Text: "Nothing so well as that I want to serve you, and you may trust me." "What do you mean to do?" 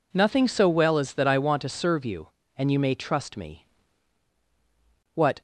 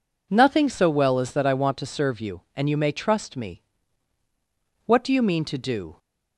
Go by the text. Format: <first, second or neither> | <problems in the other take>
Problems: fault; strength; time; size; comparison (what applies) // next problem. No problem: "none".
second | stops before "do you mean to do"; at 5.3 s